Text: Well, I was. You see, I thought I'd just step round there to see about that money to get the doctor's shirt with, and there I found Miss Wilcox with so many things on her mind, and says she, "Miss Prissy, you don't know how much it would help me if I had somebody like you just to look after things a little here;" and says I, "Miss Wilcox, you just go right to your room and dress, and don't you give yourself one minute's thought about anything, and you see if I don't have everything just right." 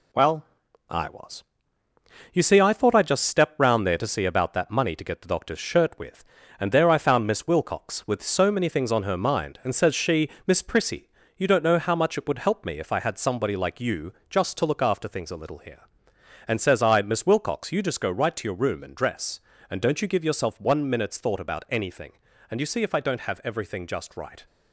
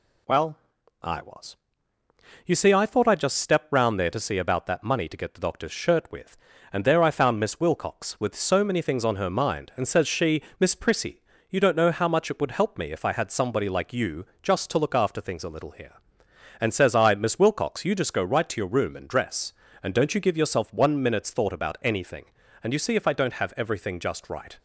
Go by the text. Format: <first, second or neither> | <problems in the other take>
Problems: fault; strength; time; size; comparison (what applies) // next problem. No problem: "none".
second | gets quieter; noticeable; throughout; 5 dB // pauses between "you" and "just"; slight; at 14.1 s; 0.18 s long; slight in the second